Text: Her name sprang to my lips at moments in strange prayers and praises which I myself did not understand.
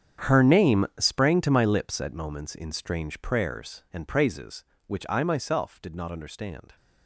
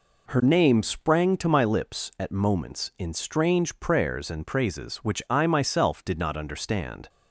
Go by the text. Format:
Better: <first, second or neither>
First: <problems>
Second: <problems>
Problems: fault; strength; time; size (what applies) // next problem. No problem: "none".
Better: second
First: gets quieter; strong; throughout; 17 dB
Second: none